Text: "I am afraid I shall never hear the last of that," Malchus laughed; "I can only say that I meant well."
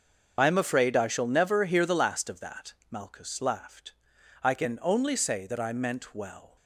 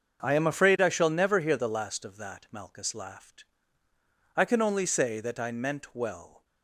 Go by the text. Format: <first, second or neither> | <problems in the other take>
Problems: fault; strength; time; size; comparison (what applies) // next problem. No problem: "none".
second | loses the start of "I"; at 0.3 s; 45 ms // starts louder than the rest; until 1.4 s; 6.5 dB; also in the second